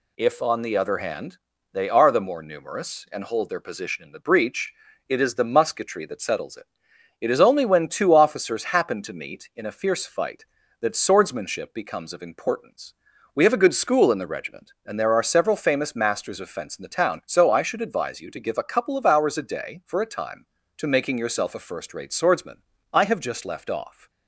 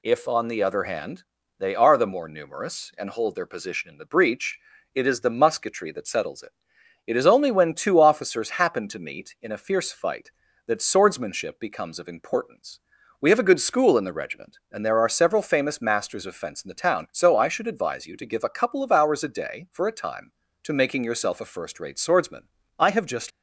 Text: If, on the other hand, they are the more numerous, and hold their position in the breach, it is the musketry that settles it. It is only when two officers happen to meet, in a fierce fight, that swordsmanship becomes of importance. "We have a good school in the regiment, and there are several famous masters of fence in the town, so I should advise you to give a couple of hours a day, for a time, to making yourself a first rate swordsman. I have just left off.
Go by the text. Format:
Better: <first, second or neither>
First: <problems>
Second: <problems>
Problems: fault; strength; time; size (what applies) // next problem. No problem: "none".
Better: first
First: none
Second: stops before "left off"; at 23.3 s